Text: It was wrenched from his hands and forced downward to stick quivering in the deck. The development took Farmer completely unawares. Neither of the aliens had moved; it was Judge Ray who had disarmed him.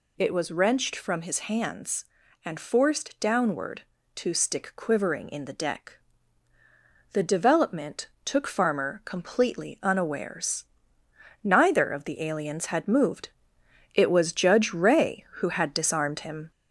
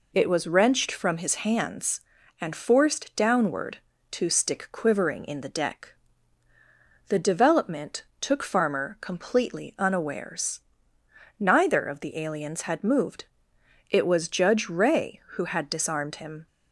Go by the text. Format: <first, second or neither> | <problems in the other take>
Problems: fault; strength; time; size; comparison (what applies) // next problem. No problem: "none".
second | gets louder; slight; throughout; 2.5 dB // pauses between "development" and "took"; slight; at 8.0 s; 0.16 s long; slight in the second